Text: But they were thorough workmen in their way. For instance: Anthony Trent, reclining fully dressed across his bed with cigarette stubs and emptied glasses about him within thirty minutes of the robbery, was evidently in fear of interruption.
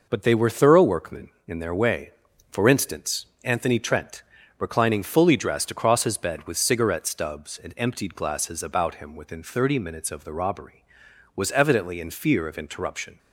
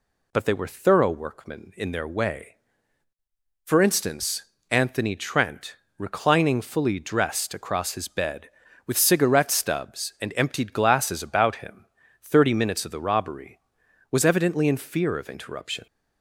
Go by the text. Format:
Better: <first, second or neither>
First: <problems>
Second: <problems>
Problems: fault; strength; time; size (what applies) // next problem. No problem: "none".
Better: first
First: none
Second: skips "within"; at 12.0 s